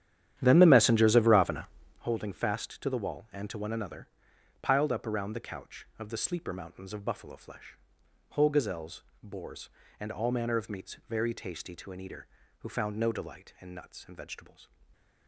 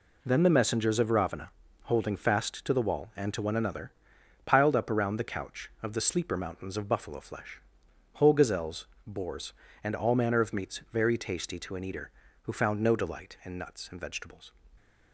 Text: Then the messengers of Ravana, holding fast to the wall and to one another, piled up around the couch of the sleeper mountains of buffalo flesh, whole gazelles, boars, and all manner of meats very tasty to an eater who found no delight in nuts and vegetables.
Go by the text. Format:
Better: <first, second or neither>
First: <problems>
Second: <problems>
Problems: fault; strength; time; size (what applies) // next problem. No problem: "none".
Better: second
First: starts louder than the rest; strong; until 2.1 s; 10.5 dB // stays silent after the last word; slight; from 14.6 s on; 0.6 s long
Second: none